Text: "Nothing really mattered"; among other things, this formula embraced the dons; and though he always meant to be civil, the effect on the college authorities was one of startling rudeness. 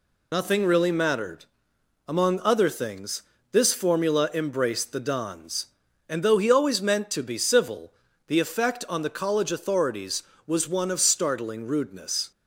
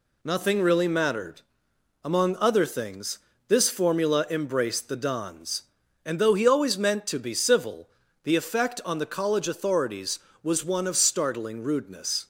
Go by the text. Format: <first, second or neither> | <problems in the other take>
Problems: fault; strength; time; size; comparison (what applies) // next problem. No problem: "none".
second | loses the start of "Nothing"; at 0.3 s; 50 ms